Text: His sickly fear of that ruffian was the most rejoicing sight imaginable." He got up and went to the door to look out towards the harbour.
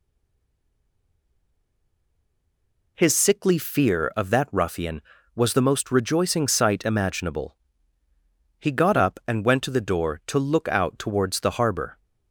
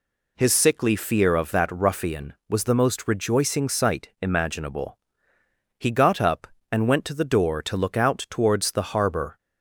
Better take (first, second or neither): second